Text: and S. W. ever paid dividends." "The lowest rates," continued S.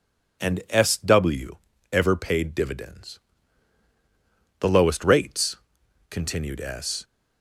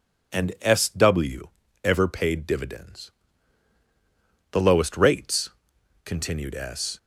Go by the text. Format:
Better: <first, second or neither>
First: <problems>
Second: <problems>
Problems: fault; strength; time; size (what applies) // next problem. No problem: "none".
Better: neither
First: pauses between "W" and "ever"; slight; at 1.5 s; 0.36 s long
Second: pauses between "W" and "ever"; slight; at 1.4 s; 0.36 s long